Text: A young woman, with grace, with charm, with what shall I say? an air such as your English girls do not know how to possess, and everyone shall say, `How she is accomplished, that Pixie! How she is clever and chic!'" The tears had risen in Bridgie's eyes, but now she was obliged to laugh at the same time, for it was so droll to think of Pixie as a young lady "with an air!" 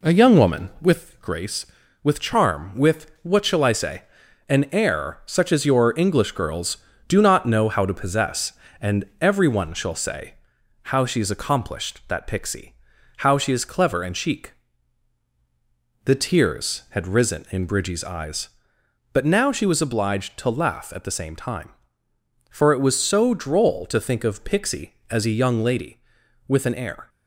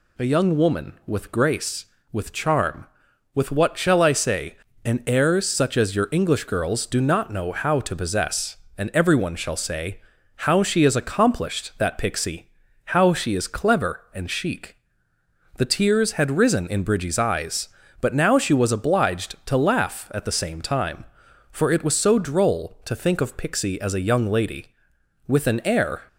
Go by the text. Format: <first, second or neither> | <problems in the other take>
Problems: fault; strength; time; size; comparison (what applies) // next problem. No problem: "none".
second | starts louder than the rest; slight; until 1.0 s; 2.5 dB